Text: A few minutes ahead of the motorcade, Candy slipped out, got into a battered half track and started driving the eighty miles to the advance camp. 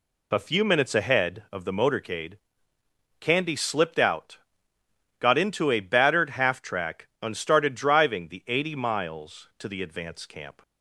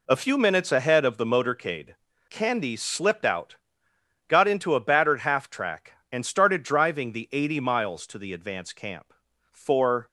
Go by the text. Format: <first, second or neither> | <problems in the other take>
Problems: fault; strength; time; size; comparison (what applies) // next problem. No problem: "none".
first | goes on to say "For"; from 9.5 s on; 0.56 s long